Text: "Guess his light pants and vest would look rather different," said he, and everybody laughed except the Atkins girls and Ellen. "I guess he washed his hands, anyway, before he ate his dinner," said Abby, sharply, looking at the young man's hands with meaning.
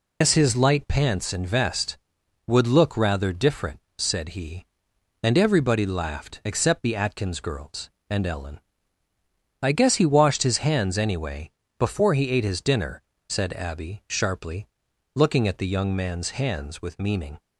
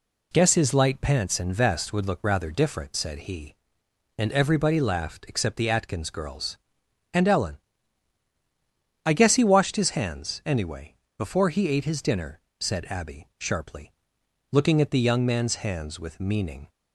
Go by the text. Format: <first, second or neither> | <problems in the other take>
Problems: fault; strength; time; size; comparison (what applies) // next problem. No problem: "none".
second | loses the start of "Guess"; at 0.2 s; 100 ms